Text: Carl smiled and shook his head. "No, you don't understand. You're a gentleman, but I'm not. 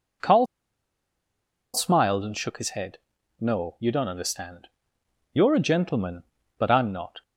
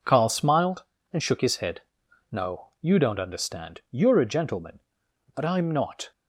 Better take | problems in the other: second | pauses between "Carl" and "smiled"; strong; at 0.4 s; 1.2 s long

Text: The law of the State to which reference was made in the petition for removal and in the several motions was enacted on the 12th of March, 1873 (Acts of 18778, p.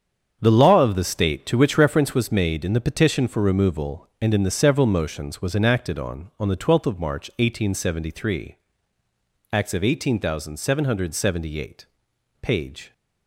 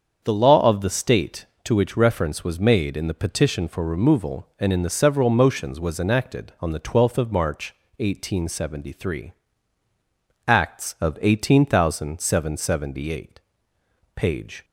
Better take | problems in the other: second | starts louder than the rest; strong; until 1.4 s; 7.5 dB; also in the second // says "on" twice; at 6.3 s

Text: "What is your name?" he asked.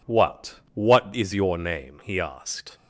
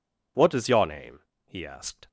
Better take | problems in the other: second | says "What" twice; at 0.7 s

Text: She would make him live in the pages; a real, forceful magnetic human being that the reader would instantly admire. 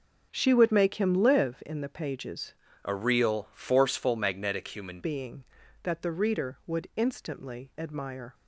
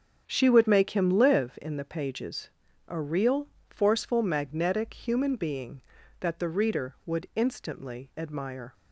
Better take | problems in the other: second | starts louder than the rest; until 1.3 s; 6.5 dB; strong in the second // changes voice from "a" to "human"; from 2.8 to 4.9 s; 2.1 s long

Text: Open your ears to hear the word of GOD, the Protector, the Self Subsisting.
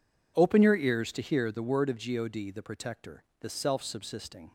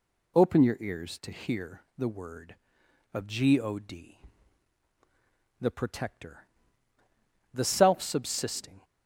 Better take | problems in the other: neither | none

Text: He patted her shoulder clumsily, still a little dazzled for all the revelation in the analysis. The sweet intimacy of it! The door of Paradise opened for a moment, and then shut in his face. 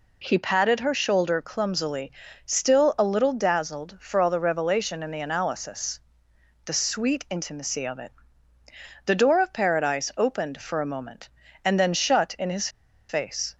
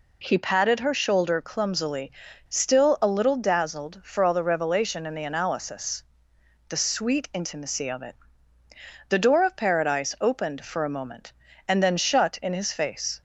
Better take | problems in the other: second | pauses between "his" and "face"; at 12.6 s; 0.40 s long

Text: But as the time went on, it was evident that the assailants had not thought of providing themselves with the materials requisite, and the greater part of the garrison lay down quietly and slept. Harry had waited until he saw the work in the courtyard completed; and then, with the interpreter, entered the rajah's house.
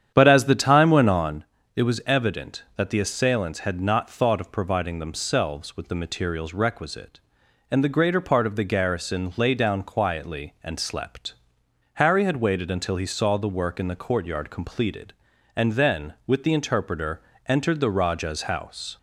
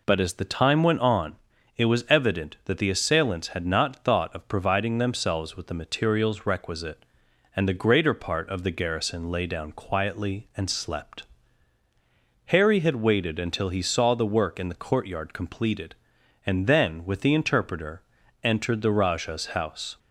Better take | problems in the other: second | starts louder than the rest; strong; until 1.4 s; 9 dB

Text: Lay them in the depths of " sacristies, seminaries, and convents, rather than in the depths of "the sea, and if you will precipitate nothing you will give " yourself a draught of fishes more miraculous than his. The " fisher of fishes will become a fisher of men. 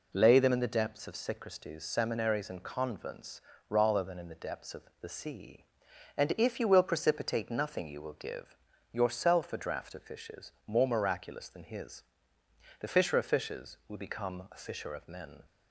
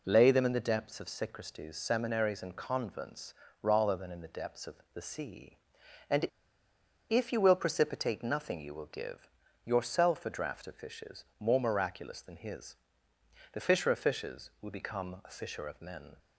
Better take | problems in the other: first | pauses between "of" and "the"; slight; at 4.7 s; 0.18 s long; slight in the first // pauses between "and" and "if"; noticeable; at 6.2 s; 0.83 s long // pauses between "fishes" and "more"; slight; at 11.2 s; 0.16 s long; slight in the first

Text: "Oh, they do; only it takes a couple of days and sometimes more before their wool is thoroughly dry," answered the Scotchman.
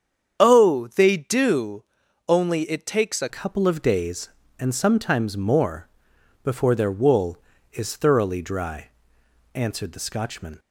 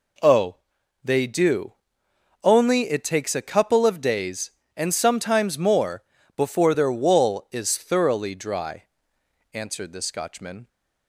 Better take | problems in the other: second | starts louder than the rest; strong; until 1.4 s; 8 dB // changes voice at "couple"; from 3.2 s on; 7.3 s long // pauses between "more" and "before"; noticeable; at 5.8 s; 0.56 s long; slight in the second

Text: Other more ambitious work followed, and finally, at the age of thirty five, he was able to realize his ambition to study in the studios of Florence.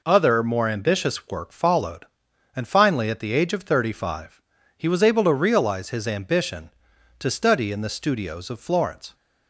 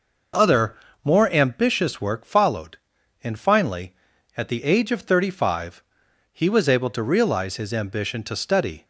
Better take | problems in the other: first | pauses between "Other" and "more"; slight; at 0.7 s; 0.30 s long // stops before "in the studios of Florence"; at 8.8 s

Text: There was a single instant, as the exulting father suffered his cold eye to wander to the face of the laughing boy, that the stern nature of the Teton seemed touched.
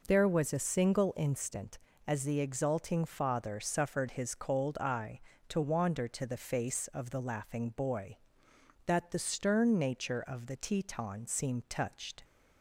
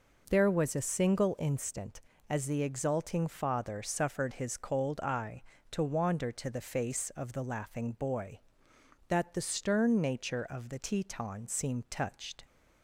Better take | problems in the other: neither | none

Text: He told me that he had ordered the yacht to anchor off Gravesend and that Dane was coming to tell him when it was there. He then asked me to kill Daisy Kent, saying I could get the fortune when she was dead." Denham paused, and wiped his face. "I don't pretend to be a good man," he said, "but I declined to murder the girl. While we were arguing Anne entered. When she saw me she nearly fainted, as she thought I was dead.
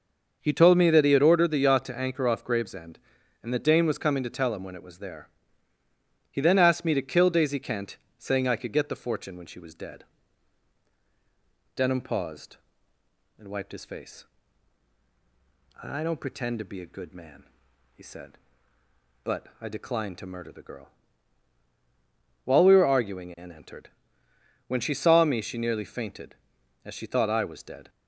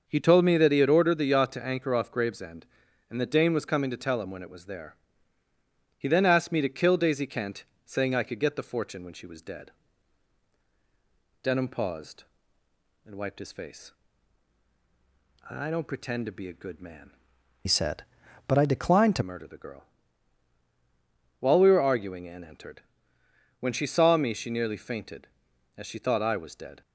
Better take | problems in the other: first | starts louder than the rest; until 1.0 s; 6.5 dB; also in the first // changes voice from "said" to "to"; from 17.6 to 19.2 s; 1.6 s long

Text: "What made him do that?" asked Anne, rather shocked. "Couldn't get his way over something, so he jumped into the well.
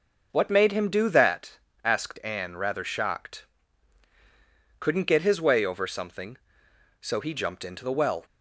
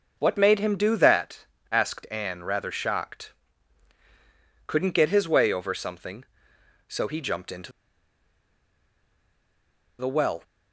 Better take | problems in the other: first | pauses between "into" and "the"; strong; at 7.7 s; 2.2 s long

